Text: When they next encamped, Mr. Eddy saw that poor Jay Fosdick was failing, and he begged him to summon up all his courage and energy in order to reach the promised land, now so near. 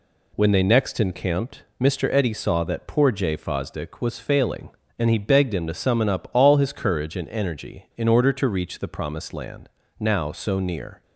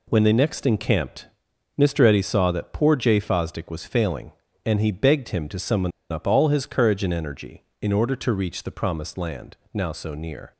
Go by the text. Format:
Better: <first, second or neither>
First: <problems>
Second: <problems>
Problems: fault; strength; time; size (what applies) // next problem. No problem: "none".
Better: first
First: none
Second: pauses between "summon" and "up"; slight; at 5.9 s; 0.21 s long